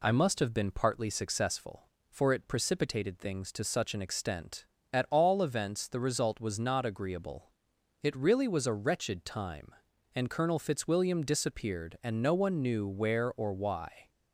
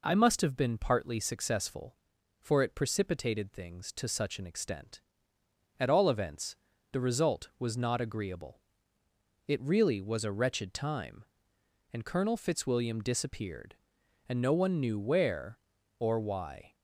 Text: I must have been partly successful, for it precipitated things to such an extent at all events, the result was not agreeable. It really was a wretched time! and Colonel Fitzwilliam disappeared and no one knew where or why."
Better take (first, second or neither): neither